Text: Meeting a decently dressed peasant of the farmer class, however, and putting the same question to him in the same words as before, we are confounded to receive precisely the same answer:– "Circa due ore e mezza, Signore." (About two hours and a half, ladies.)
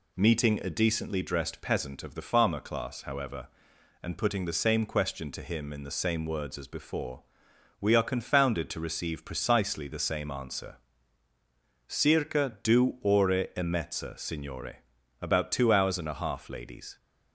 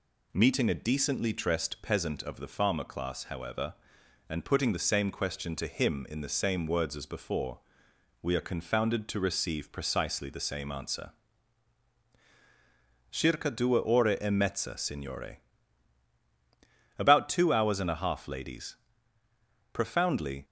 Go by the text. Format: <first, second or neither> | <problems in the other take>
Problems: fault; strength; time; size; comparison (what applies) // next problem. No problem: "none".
first | goes on to say "Profoundly"; noticeable; from 19.7 s on; 0.72 s long